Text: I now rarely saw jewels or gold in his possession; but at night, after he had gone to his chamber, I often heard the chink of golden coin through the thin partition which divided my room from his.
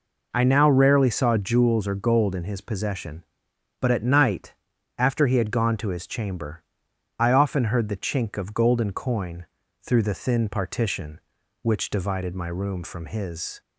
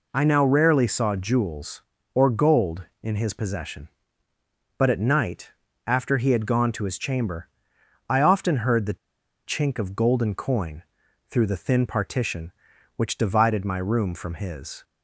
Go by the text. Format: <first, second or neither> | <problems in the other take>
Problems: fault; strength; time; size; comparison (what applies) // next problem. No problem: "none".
first | pauses between "the" and "chink"; noticeable; at 8.9 s; 0.49 s long // pauses between "coin" and "through"; noticeable; at 10.8 s; 0.48 s long; slight in the first